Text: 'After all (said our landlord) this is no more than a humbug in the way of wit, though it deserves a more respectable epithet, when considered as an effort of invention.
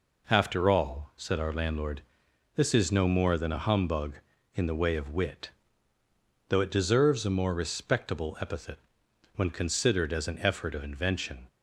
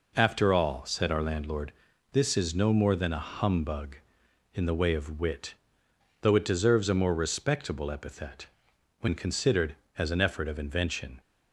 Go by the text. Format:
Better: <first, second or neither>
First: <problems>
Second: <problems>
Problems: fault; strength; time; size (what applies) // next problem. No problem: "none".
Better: neither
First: none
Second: none